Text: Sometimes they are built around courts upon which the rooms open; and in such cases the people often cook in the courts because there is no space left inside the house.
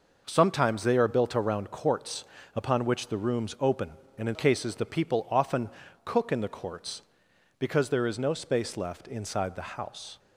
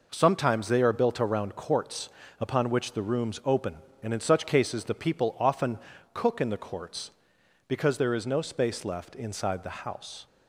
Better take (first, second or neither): second